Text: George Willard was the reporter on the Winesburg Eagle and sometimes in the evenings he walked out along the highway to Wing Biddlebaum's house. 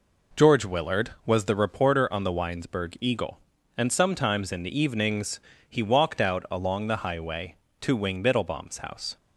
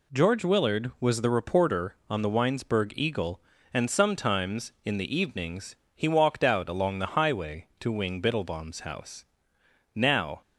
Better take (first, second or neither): first